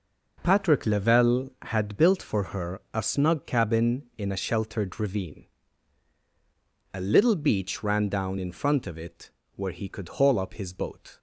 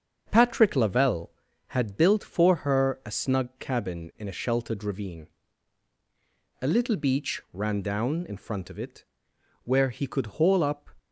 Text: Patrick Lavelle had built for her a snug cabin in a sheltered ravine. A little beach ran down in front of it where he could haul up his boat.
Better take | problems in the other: first | starts louder than the rest; until 1.3 s; 7 dB // pauses between "it" and "where"; noticeable; at 9.0 s; 0.60 s long; slight in the first // stops before "his boat"; at 10.9 s

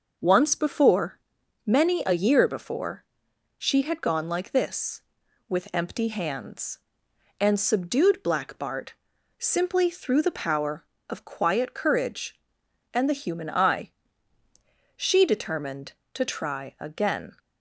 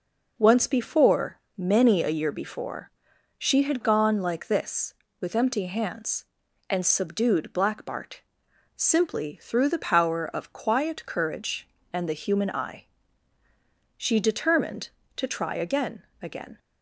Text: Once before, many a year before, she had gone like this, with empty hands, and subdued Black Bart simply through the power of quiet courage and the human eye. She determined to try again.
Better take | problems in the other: first | pauses between "Bart" and "simply"; noticeable; at 8.2 s; 0.56 s long; also in the first // says "again" twice; at 16.2 s

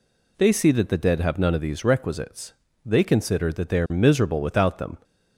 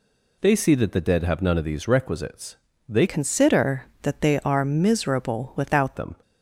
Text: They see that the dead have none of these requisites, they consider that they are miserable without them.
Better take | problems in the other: first | changes voice from "consider" to "without"; from 3.0 to 5.9 s; 2.9 s long

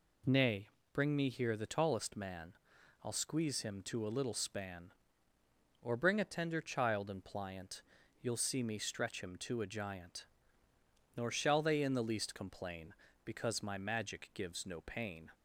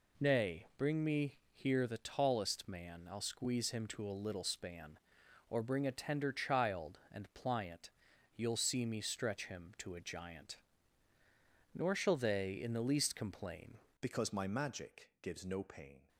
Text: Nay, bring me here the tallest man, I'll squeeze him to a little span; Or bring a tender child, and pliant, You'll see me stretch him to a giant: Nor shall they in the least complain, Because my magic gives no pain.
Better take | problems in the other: first | pauses between "me" and "here"; slight; at 1.3 s; 0.16 s long // changes voice at "Because"; from 13.9 s on; 2.1 s long

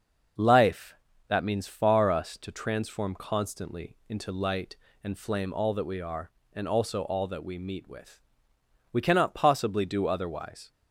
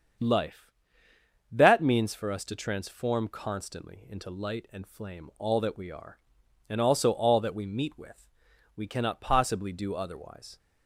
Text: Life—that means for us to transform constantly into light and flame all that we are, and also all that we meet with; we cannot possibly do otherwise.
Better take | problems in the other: second | starts louder than the rest; noticeable; until 1.7 s; 6 dB; strong in the second // says "far" for "for"; at 1.6 s

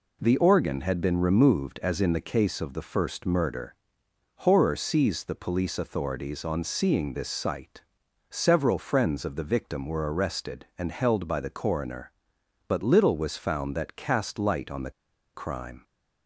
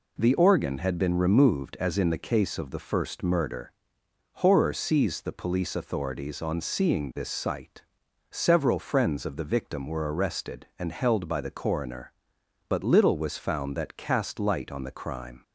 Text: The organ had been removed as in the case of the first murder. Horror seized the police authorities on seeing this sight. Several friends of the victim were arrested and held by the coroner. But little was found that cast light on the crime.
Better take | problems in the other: second | pauses between "the" and "crime"; at 14.8 s; 0.44 s long

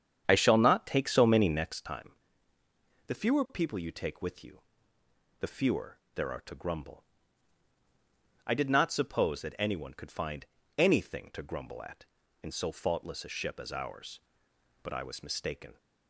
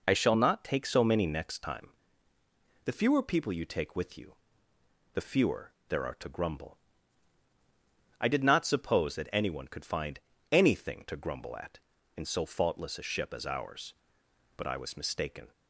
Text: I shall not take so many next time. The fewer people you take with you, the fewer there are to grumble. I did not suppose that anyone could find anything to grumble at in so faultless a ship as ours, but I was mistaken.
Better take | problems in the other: second | starts louder than the rest; strong; until 1.8 s; 8.5 dB // pauses between "fewer" and "there"; slight; at 5.9 s; 0.16 s long; slight in the second // pauses between "find" and "anything"; slight; at 10.4 s; 0.32 s long; slight in the second

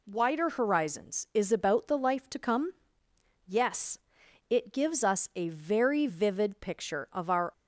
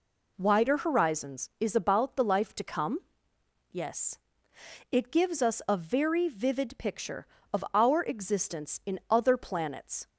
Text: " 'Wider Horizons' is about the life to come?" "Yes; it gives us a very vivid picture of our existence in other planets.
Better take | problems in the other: second | stops before "existence in other planets"; at 7.5 s

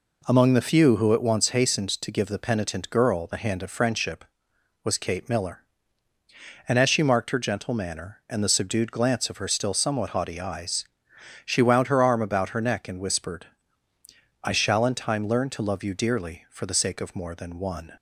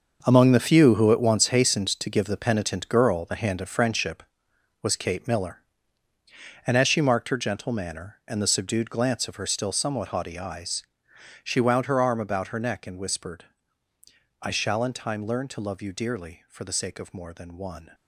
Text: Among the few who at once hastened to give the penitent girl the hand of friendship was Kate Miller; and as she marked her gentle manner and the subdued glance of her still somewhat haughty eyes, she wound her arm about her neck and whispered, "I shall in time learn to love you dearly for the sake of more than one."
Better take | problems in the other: first | gets quieter; strong; throughout; 12.5 dB

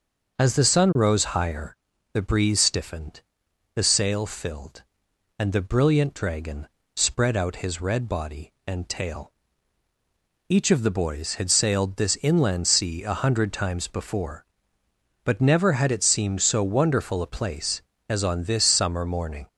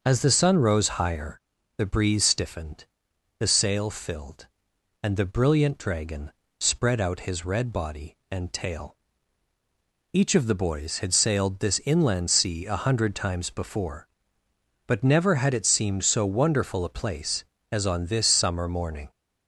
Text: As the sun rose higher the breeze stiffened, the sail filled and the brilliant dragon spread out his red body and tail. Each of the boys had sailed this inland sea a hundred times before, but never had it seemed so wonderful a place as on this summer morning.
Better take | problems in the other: neither | starts louder than the rest; the same in both // pauses between "higher" and "the"; the same in both // pauses between "dragon" and "spread"; slight; the same in both

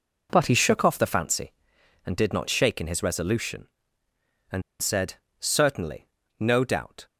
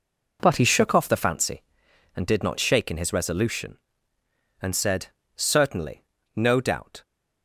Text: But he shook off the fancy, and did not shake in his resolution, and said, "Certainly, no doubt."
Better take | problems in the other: second | pauses between "and" and "said"; slight; at 4.6 s; 0.20 s long

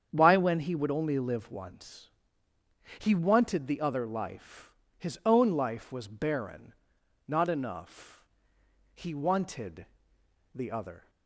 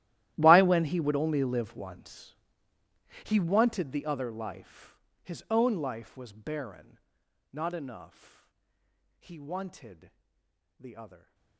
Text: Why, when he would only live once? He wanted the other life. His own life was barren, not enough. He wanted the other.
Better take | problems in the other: first | gets quieter; strong; throughout; 21.5 dB // starts louder than the rest; strong; until 1.3 s; 14 dB; strong in the first // pauses between "wanted" and "the"; noticeable; at 10.1 s; 0.68 s long; noticeable in the first

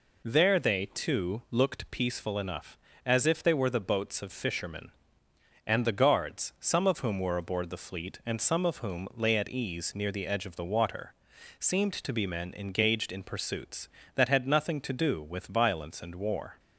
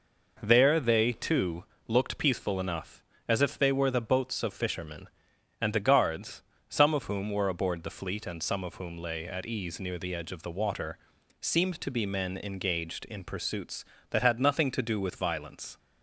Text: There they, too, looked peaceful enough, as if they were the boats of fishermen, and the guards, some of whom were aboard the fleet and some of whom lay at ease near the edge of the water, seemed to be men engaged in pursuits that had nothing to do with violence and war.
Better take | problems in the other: first | stops before "and war"; at 15.7 s

